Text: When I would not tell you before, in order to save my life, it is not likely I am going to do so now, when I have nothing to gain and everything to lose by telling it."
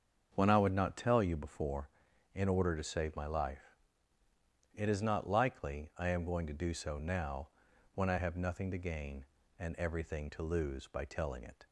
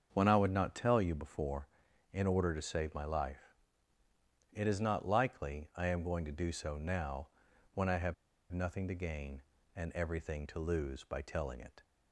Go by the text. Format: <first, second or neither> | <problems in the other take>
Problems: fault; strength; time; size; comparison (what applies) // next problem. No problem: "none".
first | starts louder than the rest; until 1.1 s; 7 dB; also in the first // pauses between "have" and "nothing"; at 8.1 s; 0.38 s long